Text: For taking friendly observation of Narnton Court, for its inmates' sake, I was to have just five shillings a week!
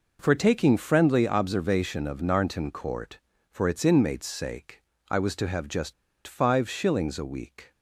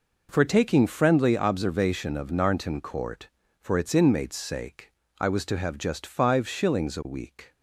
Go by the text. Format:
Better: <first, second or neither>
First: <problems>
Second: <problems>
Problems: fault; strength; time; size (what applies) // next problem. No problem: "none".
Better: second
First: pauses between "just" and "five"; slight; at 5.9 s; 0.33 s long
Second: none